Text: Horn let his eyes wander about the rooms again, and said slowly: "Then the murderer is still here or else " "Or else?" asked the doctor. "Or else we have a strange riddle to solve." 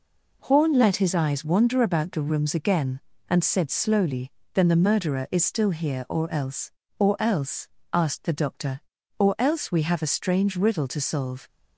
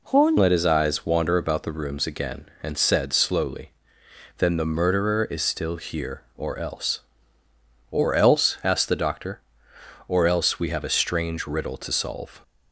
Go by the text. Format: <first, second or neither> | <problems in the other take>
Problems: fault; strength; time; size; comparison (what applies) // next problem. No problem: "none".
first | changes voice at "let"; from 0.3 s on; 12.1 s long